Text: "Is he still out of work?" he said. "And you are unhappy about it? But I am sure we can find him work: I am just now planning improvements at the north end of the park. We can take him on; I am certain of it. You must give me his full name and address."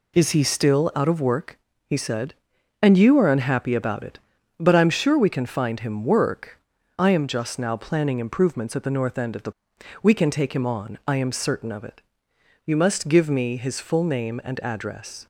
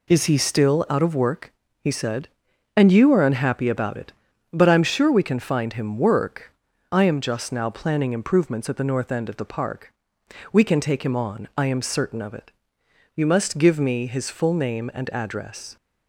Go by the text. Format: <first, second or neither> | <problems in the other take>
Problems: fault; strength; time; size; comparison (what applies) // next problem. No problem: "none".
second | skips "park"; at 9.7 s